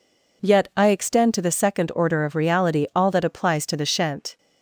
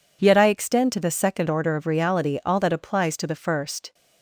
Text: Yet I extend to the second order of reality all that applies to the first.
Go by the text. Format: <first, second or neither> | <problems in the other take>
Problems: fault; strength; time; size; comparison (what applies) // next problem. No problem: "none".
second | says "shent" for "first"; at 3.8 s